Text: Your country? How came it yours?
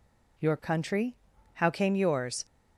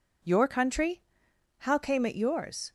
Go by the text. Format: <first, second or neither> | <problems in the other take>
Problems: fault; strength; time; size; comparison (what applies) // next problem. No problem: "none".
second | skips "it"; at 1.9 s